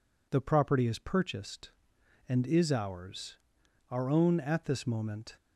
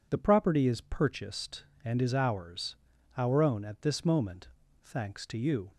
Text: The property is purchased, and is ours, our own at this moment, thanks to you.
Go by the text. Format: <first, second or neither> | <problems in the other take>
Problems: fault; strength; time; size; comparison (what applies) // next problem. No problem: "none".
second | stops before "thanks to you"; at 5.3 s